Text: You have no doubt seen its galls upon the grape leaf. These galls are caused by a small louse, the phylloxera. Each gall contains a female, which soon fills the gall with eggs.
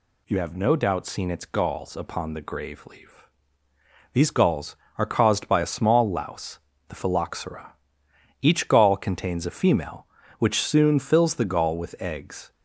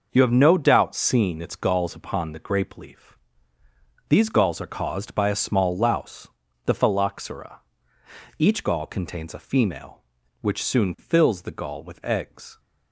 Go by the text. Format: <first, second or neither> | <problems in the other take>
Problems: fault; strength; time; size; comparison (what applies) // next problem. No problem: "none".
second | says "grave" for "grape"; at 2.4 s